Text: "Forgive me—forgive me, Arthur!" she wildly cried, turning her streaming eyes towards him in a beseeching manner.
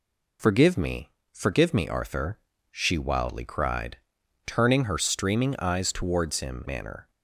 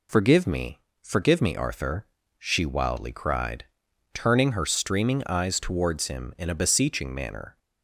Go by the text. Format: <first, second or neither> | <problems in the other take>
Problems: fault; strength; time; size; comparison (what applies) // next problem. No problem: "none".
second | skips "in a beseeching"; at 6.6 s